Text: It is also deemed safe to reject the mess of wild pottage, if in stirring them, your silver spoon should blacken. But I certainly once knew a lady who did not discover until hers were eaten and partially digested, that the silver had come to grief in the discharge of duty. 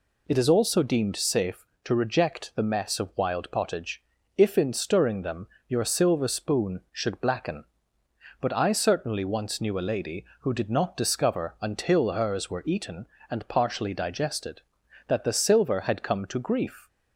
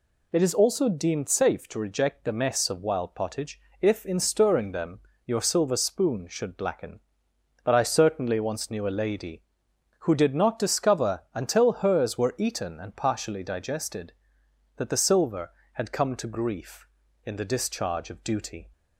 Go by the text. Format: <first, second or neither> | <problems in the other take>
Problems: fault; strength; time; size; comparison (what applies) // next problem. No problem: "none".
second | stops before "in the discharge of duty"; at 16.8 s